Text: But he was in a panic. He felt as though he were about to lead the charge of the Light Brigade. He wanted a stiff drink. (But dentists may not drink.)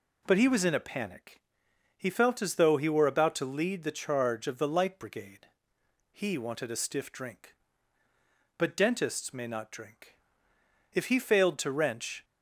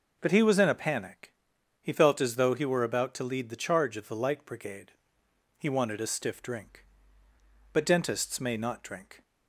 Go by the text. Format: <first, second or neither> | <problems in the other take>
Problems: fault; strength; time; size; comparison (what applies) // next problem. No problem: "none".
second | goes on to say "If he failed to wrench"; noticeable; from 10.9 s on; 1.3 s long